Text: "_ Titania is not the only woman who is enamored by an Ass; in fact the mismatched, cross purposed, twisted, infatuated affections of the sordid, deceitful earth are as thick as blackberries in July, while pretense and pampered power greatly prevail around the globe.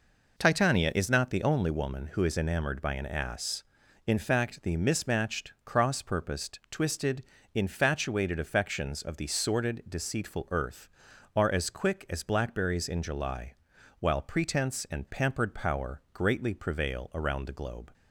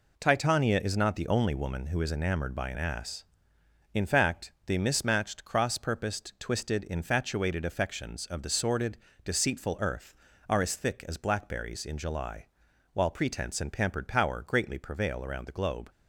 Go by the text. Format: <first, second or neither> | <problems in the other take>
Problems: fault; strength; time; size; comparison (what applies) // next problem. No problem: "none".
second | says "quick" for "thick"; at 11.7 s